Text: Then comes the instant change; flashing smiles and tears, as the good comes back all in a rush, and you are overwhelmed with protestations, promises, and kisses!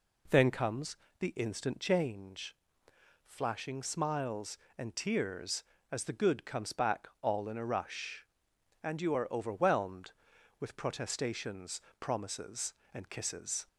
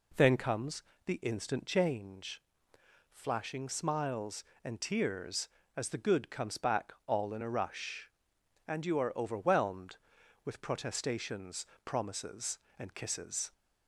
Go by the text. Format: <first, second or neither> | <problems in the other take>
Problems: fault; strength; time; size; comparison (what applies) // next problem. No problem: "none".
neither | pauses between "comes" and "the"; slight; the same in both // pauses between "back" and "all"; slight; the same in both